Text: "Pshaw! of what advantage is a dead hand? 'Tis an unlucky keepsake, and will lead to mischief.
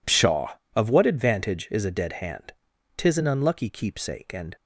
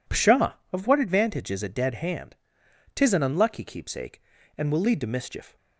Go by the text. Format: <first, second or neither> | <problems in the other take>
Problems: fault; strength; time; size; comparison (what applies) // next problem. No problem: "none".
second | stops before "will lead to mischief"; at 4.5 s